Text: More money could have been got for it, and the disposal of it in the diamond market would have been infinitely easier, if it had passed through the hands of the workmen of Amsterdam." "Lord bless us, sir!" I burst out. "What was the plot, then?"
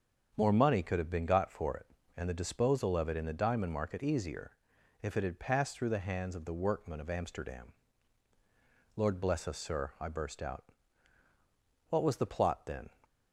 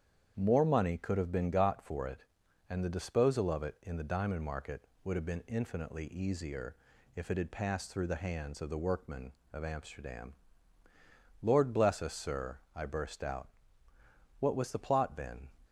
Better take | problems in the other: second | starts louder than the rest; strong; until 1.3 s; 7 dB; strong in the second // skips "would have been infinitely"; at 4.0 s

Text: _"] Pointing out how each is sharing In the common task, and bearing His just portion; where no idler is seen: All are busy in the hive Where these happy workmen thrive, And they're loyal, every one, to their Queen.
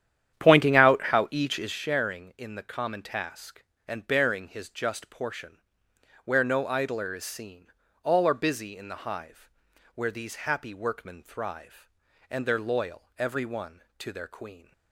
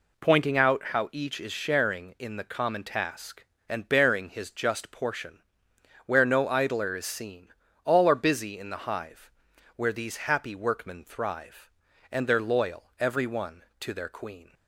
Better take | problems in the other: second | starts louder than the rest; strong; until 1.8 s; 10 dB // pauses between "hive" and "Where"; noticeable; at 9.4 s; 0.46 s long; noticeable in the second

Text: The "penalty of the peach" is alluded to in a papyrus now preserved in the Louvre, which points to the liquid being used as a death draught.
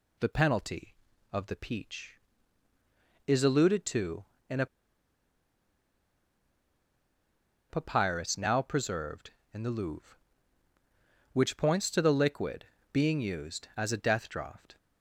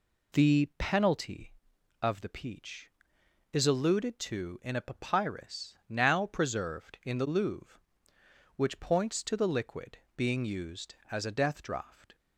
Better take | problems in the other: second | pauses between "a" and "papyrus"; strong; at 4.6 s; 3.0 s long // pauses between "liquid" and "being"; slight; at 12.6 s; 0.26 s long; slight in the second

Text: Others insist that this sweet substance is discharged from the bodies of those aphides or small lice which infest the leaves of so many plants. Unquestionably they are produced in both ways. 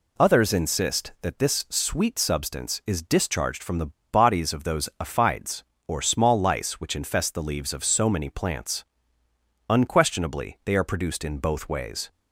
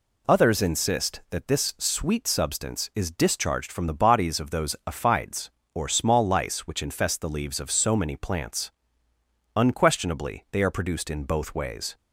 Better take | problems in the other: second | pauses between "the" and "bodies"; slight; at 3.9 s; 0.21 s long

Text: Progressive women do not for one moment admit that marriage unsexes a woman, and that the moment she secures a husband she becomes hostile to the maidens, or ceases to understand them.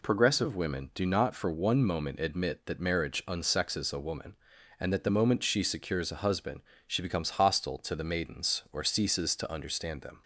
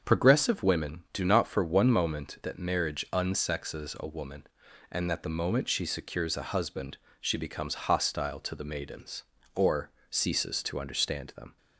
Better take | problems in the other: first | starts louder than the rest; until 1.0 s; 7 dB // skips "admit"; at 2.4 s // pauses between "husband" and "she"; slight; at 6.9 s; 0.24 s long; slight in the first // pauses between "or" and "ceases"; slight; at 9.9 s; 0.18 s long

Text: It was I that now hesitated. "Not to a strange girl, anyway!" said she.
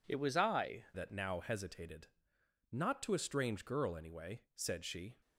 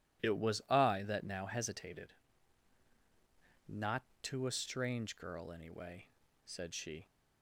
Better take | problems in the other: second | changes voice at "that"; from 0.9 s on; 4.2 s long

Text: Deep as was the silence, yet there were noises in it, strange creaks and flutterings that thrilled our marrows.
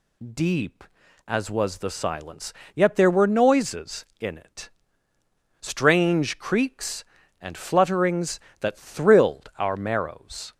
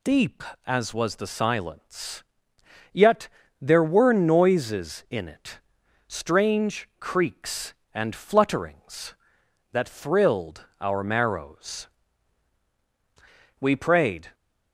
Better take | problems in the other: first | pauses between "yet" and "there"; slight; at 3.2 s; 0.34 s long // goes on to say "We prayed"; noticeable; from 13.6 s on; 0.72 s long

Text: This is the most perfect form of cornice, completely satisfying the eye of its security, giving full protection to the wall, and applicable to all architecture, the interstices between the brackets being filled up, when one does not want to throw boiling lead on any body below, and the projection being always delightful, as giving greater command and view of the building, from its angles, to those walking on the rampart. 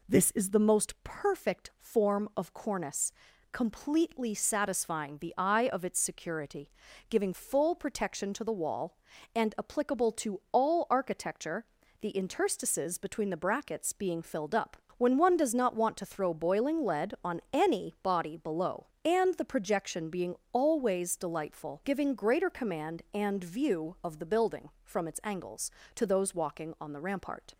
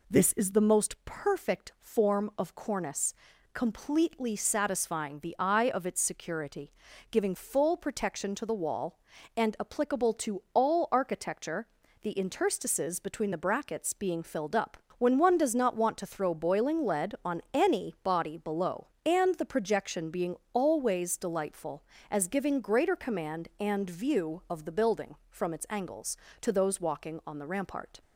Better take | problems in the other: second | pauses between "being" and "always"; slight; at 20.3 s; 0.16 s long; slight in the second // skips "as"; at 21.8 s

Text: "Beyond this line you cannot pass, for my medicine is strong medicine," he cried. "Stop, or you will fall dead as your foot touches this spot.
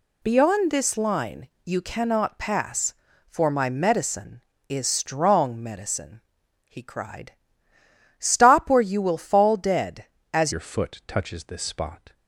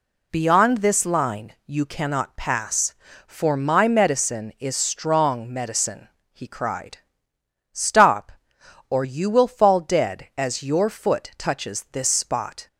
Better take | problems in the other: second | pauses between "line" and "you"; slight; at 1.4 s; 0.16 s long // changes voice at "your"; from 10.5 s on; 1.6 s long

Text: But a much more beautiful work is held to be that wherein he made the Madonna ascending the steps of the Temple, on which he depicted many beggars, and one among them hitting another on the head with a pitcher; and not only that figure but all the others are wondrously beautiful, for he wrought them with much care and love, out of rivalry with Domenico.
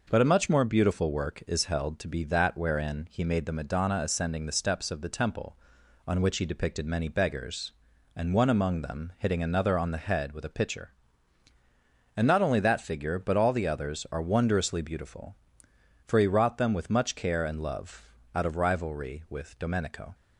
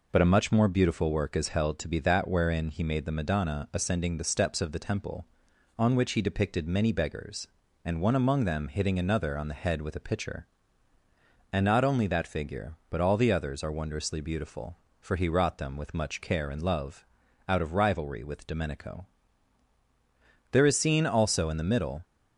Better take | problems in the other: first | goes on to say "There is seen also in the middle"; from 20.4 s on; 1.5 s long

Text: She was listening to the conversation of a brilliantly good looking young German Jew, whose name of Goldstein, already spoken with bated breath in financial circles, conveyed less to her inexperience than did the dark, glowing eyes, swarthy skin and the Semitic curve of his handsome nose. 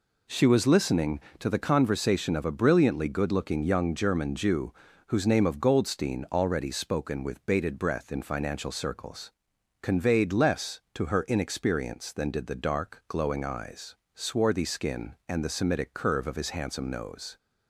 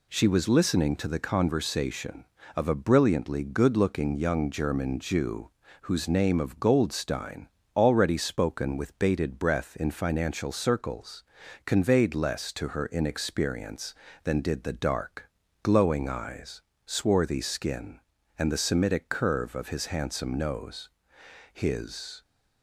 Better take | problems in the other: first | goes on to say "His"; noticeable; from 21.5 s on; 0.68 s long

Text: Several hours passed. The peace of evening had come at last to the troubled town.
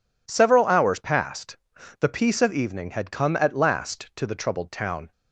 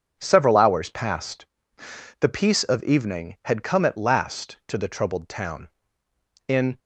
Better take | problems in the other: first | goes on to say "In"; slight; from 6.4 s on; 0.32 s long

